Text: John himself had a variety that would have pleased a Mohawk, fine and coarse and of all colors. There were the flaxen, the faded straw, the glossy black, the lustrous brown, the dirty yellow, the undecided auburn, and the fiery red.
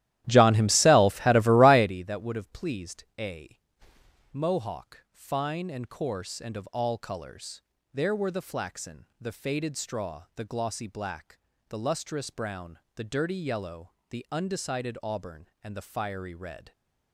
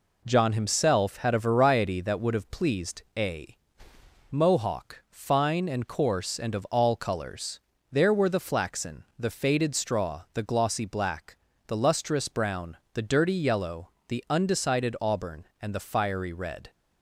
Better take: second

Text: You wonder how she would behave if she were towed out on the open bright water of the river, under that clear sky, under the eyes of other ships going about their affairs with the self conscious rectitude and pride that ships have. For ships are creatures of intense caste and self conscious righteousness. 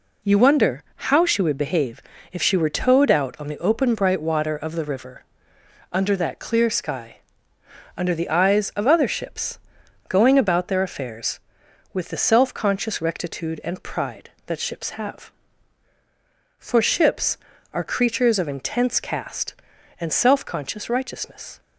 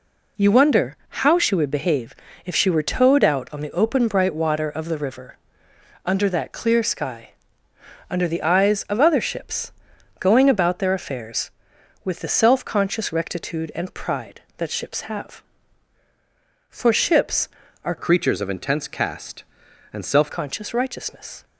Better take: first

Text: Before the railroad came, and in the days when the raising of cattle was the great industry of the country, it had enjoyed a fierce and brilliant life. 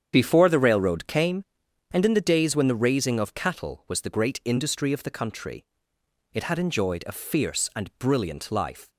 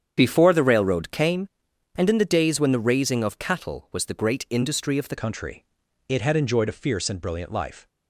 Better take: first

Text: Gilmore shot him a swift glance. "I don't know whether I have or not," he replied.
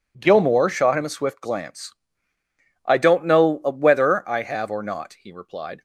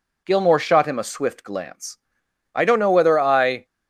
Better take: first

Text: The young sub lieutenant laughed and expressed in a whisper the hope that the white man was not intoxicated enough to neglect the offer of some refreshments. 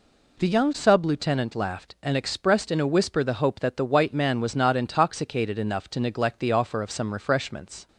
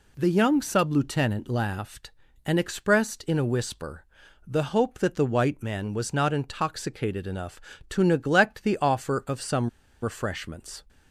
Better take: first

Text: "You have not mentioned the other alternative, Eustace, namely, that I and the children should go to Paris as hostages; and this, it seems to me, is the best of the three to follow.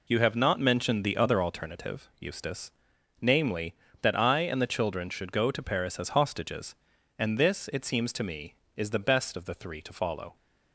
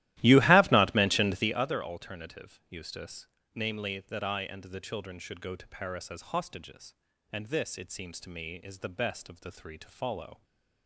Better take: first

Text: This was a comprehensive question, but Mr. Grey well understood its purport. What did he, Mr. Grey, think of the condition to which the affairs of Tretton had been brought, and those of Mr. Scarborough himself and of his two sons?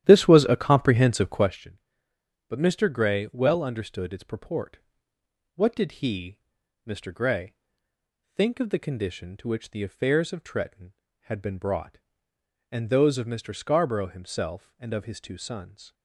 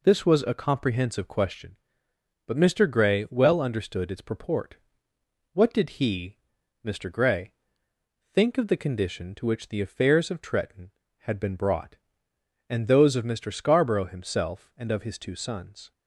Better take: second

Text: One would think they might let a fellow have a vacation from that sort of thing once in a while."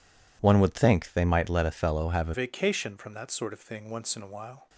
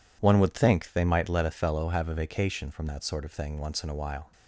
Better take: second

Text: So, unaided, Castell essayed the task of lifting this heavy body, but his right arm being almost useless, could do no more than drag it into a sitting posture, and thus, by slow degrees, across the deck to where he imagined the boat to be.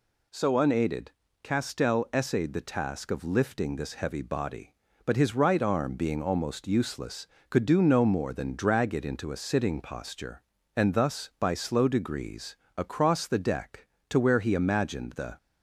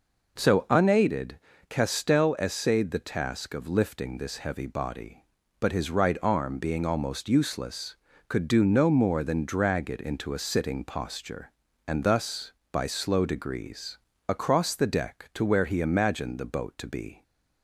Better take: second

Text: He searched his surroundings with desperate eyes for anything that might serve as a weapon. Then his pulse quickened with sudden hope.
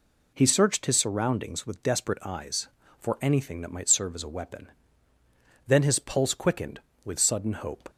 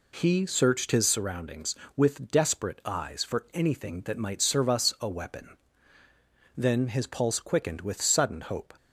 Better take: first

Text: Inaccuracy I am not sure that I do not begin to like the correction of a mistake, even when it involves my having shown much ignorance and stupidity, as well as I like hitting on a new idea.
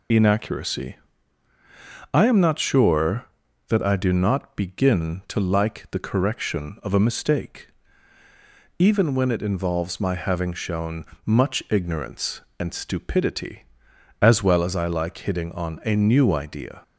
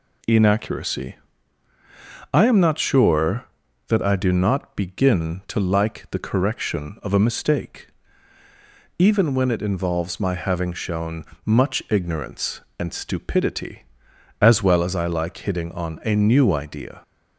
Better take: second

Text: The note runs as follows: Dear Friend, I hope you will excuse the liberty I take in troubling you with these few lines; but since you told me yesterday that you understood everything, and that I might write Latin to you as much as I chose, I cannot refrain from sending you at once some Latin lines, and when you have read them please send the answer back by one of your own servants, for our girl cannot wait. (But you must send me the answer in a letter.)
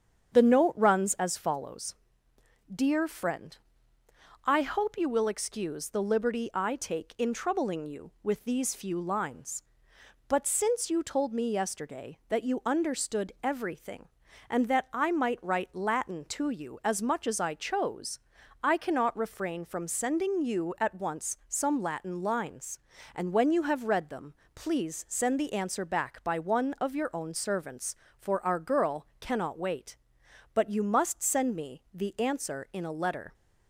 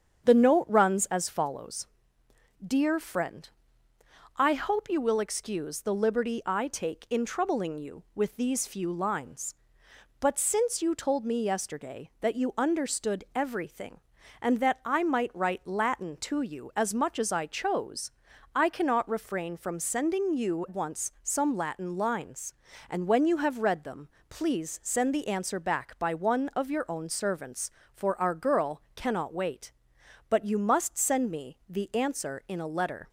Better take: first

